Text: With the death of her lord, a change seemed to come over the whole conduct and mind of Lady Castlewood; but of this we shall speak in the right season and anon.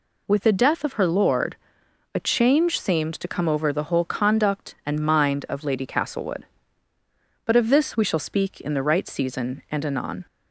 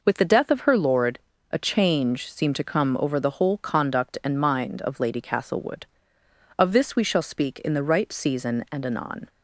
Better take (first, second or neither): first